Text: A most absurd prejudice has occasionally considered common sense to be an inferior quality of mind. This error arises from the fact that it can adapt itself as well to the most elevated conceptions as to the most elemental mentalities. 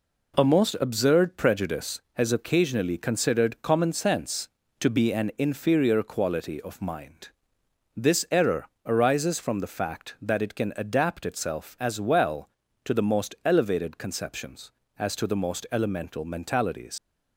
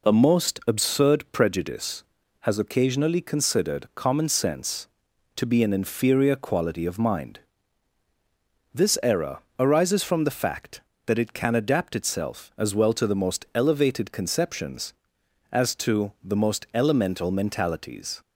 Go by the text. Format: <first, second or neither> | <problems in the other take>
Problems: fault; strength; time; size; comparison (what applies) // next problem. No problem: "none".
second | pauses between "error" and "arises"; slight; at 8.6 s; 0.18 s long; slight in the second // leaves "mentalities" unfinished; at 16.9 s; 85 ms